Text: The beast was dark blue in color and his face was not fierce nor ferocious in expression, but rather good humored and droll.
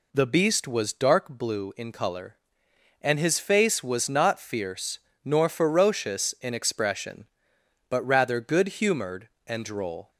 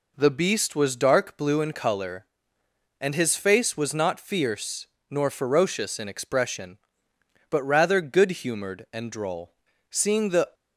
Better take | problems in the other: first | pauses between "fierce" and "nor"; slight; at 4.8 s; 0.24 s long; slight in the first // goes on to say "Seeing the"; noticeable; from 9.8 s on; 0.64 s long

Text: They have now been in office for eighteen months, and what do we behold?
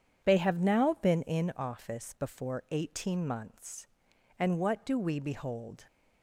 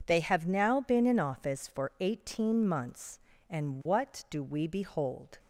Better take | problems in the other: second | says "before" for "for"; at 2.1 s

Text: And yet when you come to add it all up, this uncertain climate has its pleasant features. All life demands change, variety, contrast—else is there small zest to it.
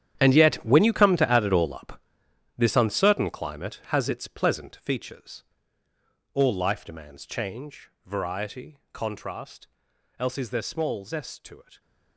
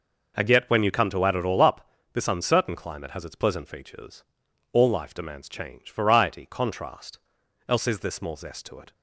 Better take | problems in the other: second | gets quieter; strong; throughout; 14.5 dB

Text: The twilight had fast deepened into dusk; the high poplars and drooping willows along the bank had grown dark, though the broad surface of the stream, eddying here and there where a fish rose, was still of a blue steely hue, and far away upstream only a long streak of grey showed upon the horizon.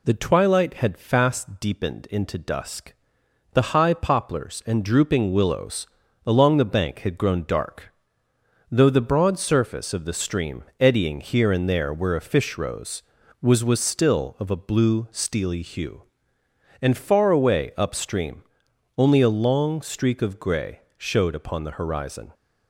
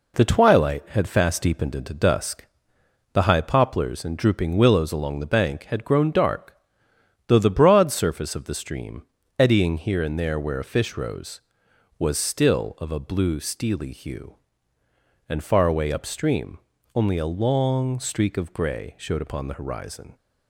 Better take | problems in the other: second | pauses between "willows" and "along"; at 5.8 s; 0.40 s long // says "was" twice; at 13.6 s // pauses between "upstream" and "only"; noticeable; at 18.4 s; 0.54 s long; slight in the second // pauses between "grey" and "showed"; slight; at 20.8 s; 0.16 s long

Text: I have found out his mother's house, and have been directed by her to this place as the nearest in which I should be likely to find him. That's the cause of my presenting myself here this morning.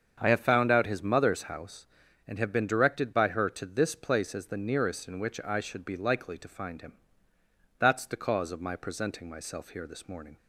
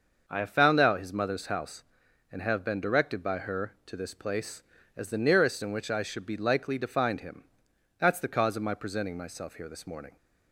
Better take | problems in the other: neither | starts louder than the rest; the same in both

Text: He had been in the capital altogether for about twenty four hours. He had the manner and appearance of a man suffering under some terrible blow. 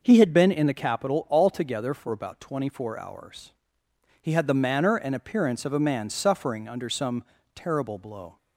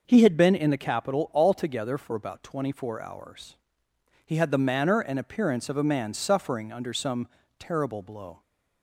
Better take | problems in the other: neither | pauses between "some" and "terrible"; slight; the same in both

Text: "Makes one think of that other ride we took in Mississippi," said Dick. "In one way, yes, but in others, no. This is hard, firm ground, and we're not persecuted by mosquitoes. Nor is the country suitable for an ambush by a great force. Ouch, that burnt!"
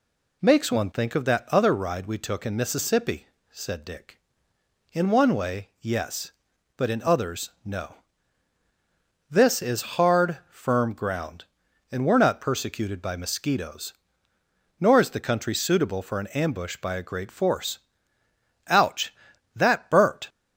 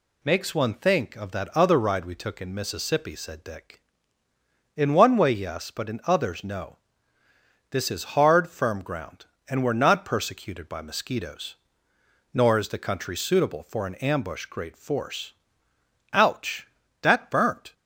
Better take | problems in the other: first | skips "by a"; at 14.4 s

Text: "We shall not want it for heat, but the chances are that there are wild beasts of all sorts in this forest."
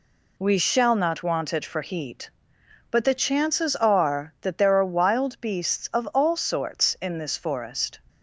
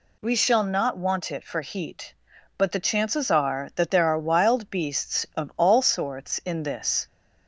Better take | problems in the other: first | stops before "forest"; at 7.0 s

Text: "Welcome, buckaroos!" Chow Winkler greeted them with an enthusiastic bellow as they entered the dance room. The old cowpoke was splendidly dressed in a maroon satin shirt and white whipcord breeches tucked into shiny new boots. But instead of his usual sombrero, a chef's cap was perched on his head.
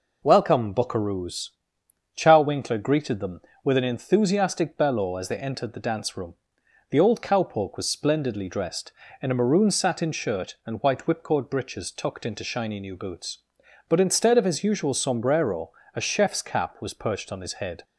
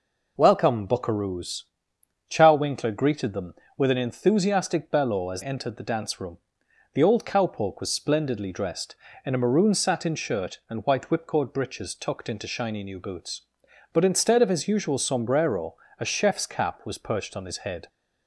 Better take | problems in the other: first | skips "they"; at 5.4 s

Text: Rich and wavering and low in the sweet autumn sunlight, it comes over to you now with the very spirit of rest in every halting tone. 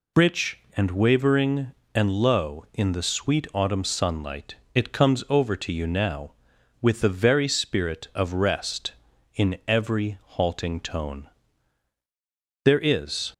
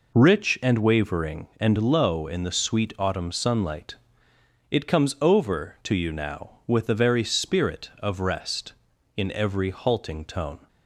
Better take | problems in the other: second | pauses between "every" and "halting"; slight; at 10.1 s; 0.16 s long // goes on to say "There is"; noticeable; from 12.6 s on; 0.68 s long

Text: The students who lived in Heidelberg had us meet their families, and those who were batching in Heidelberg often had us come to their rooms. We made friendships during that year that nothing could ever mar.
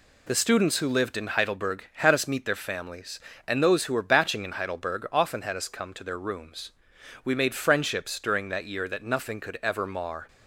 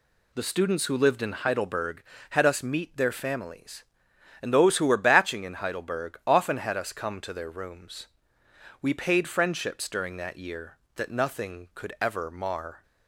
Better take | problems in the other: first | says "paid" for "made"; at 8.9 s

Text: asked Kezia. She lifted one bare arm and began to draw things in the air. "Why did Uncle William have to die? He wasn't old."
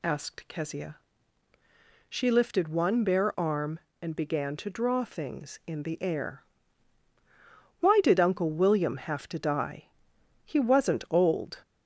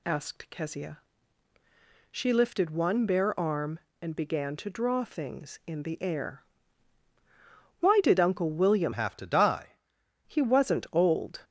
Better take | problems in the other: first | changes voice from "have" to "die"; from 8.9 to 9.7 s; 0.8 s long

